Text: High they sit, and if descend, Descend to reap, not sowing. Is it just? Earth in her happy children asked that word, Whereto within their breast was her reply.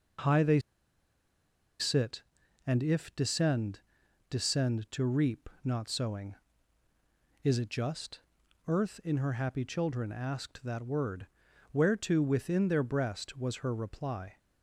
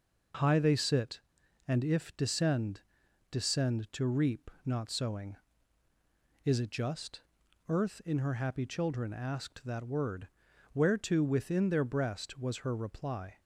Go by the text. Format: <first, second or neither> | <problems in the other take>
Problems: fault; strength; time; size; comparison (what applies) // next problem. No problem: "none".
second | pauses between "they" and "sit"; at 0.5 s; 1.2 s long